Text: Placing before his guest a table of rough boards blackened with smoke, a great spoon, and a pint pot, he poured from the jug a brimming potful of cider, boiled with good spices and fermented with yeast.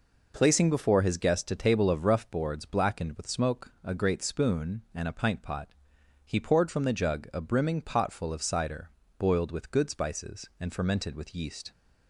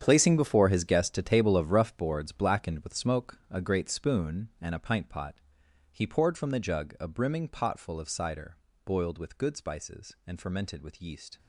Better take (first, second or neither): first